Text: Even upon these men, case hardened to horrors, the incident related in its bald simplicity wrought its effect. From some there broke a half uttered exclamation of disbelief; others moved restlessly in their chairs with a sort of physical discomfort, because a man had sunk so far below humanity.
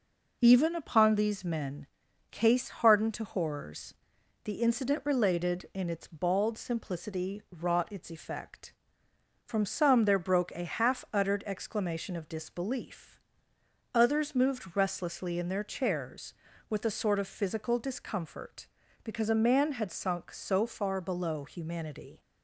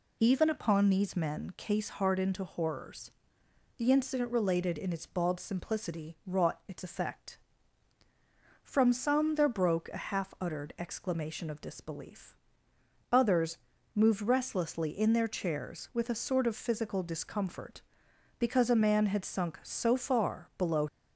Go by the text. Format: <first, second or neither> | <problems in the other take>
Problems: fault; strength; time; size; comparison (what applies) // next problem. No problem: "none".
first | pauses between "others" and "moved"; slight; at 13.5 s; 0.36 s long // stops before "humanity"; at 20.8 s